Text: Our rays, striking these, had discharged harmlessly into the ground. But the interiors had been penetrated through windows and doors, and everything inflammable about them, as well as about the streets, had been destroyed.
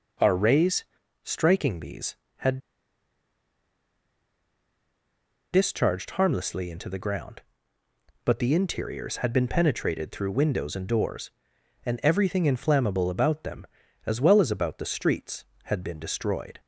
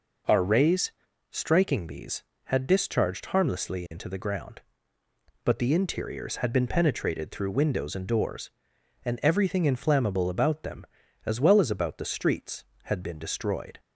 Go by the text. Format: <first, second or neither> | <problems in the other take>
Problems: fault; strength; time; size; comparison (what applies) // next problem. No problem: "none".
second | pauses between "had" and "discharged"; strong; at 2.5 s; 2.9 s long